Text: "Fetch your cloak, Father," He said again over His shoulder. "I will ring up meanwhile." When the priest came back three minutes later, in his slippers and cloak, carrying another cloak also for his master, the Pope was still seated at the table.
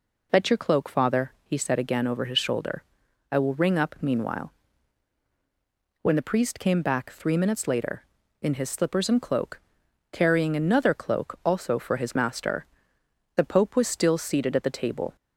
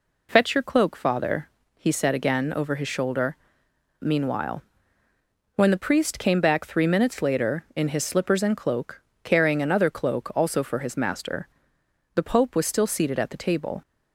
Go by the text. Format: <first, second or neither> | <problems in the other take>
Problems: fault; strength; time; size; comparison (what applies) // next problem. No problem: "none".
first | skips "I will ring up"; at 3.6 s